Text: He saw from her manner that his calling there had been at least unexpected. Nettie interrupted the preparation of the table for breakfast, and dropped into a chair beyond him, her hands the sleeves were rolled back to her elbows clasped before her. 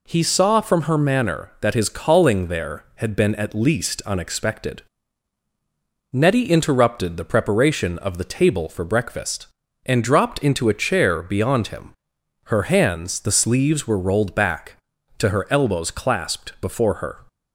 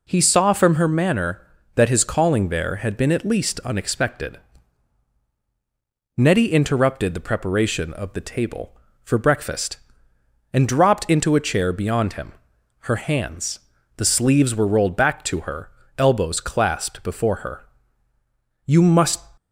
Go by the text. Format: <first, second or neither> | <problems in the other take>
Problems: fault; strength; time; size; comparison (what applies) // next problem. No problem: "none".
first | pauses between "hands" and "the"; at 13.5 s; 0.38 s long // pauses between "her" and "elbows"; slight; at 15.6 s; 0.28 s long // goes on to say "You must"; noticeable; from 18.6 s on; 0.62 s long